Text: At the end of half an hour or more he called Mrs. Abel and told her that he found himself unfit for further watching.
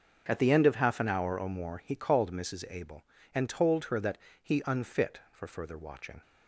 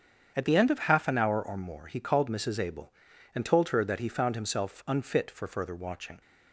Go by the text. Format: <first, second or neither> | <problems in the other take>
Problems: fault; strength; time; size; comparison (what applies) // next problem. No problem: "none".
second | starts louder than the rest; until 1.2 s; 7 dB; strong in the second // pauses between "that" and "he"; slight; at 4.1 s; 0.26 s long // skips "found himself"; at 4.6 s